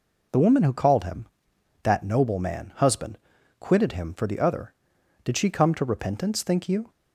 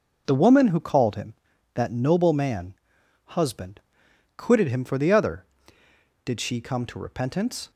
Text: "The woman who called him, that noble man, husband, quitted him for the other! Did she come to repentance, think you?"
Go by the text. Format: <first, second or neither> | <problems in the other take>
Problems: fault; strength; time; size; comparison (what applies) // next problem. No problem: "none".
first | stops before "think you"; at 7.7 s